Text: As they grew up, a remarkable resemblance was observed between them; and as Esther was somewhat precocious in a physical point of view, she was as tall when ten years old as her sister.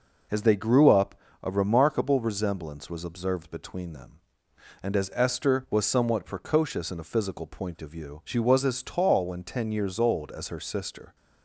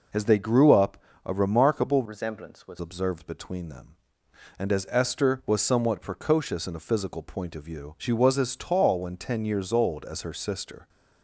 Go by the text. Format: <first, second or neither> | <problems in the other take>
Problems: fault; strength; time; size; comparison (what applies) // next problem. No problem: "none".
first | changes voice from "resemblance" to "was"; from 2.0 to 2.7 s; 0.7 s long